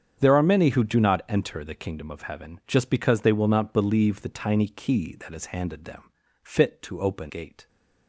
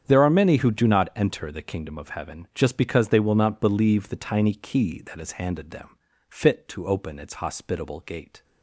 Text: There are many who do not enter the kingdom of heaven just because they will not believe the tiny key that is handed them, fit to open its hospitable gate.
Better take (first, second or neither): second